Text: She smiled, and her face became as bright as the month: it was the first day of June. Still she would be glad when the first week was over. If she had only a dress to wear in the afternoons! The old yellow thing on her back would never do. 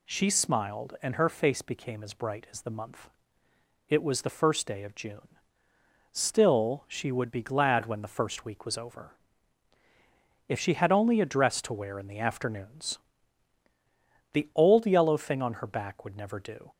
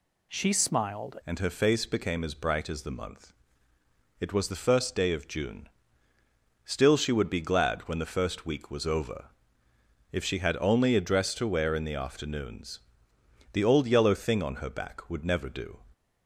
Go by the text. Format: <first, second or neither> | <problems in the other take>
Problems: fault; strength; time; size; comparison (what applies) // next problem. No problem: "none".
first | changes voice at "and"; from 1.2 s on; 14.5 s long